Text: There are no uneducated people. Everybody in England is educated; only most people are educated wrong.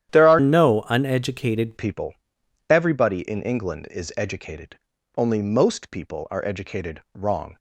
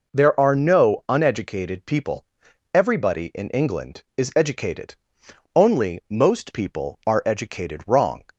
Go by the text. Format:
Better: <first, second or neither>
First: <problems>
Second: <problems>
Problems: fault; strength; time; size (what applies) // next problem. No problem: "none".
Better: second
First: starts louder than the rest; strong; until 1.1 s; 11 dB // changes voice from "no" to "uneducated"; from 0.3 to 1.7 s; 1.4 s long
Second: none